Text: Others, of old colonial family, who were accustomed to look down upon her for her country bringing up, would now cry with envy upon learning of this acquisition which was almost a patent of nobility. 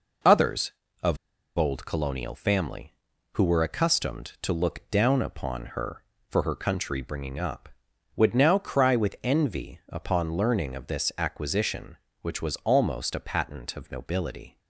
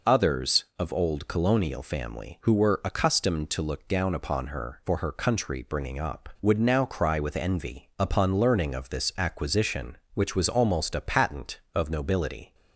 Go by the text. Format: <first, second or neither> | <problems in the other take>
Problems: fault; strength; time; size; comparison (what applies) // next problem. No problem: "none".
second | pauses between "of" and "old"; at 1.1 s; 0.39 s long